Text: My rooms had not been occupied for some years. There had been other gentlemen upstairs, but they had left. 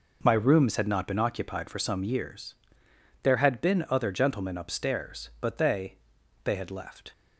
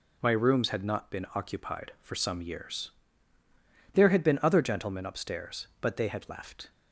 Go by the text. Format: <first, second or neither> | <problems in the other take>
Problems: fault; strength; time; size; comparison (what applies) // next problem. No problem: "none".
second | says "they" twice; at 6.4 s